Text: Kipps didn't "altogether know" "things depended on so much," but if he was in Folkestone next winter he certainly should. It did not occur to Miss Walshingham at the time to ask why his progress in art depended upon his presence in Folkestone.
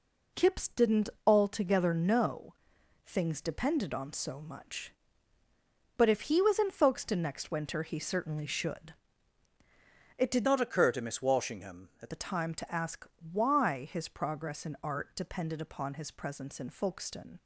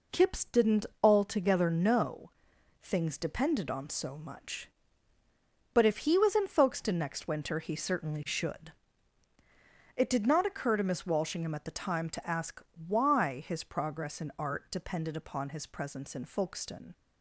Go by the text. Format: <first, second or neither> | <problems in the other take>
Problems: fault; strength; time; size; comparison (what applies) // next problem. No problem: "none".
second | pauses between "didn't" and "altogether"; slight; at 1.0 s; 0.18 s long; slight in the second // pauses between "know" and "things"; noticeable; at 2.5 s; 0.52 s long; noticeable in the second // changes voice from "not" to "at"; from 10.4 to 12.1 s; 1.7 s long // pauses between "ask" and "why"; slight; at 13.0 s; 0.24 s long; slight in the second